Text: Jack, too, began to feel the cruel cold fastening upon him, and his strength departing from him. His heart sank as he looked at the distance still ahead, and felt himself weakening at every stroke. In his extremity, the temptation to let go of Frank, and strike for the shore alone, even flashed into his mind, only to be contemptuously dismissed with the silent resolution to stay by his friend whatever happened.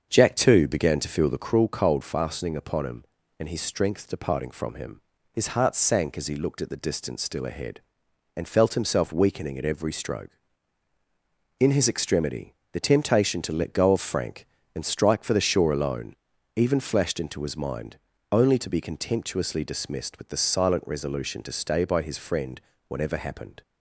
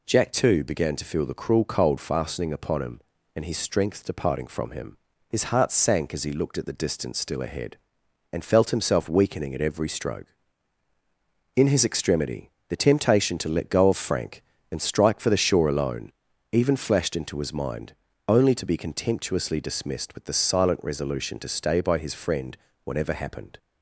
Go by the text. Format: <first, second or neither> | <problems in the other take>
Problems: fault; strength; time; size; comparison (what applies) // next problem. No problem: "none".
second | starts louder than the rest; until 1.7 s; 7 dB // pauses between "friend" and "whatever"; slight; at 22.5 s; 0.28 s long; slight in the second